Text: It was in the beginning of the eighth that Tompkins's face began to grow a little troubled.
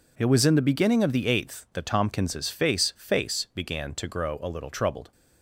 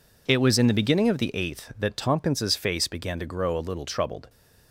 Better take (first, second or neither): second